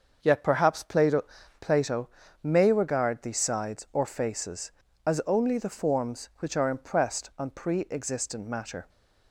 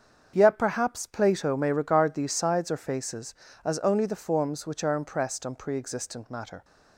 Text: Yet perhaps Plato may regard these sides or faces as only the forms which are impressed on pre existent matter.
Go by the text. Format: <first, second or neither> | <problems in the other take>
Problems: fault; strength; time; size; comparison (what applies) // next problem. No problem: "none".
second | starts louder than the rest; until 1.2 s; 6.5 dB; strong in the second // says "Plato" twice; at 1.6 s